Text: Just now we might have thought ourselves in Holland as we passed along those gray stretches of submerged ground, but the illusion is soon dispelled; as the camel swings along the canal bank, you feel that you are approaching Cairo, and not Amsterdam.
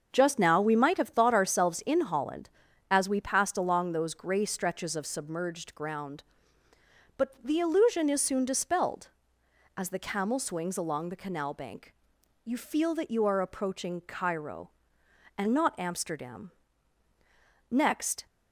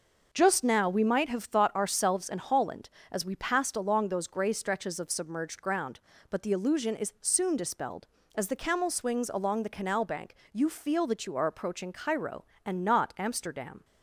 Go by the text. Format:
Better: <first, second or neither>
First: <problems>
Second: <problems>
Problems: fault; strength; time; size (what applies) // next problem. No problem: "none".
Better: second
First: starts louder than the rest; until 1.1 s; 6.5 dB // goes on to say "Next"; from 17.6 s on; 0.56 s long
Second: none